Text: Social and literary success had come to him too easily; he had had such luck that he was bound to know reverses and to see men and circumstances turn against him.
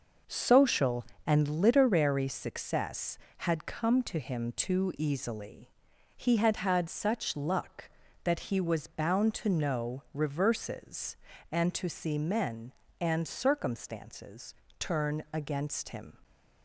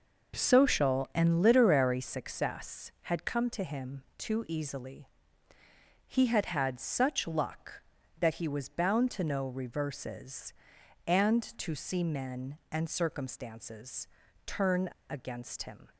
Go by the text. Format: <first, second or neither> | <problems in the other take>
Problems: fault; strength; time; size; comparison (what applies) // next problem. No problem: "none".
first | pauses between "circumstances" and "turn"; slight; at 14.0 s; 0.36 s long; slight in the first // pauses between "turn" and "against"; slight; at 14.8 s; 0.20 s long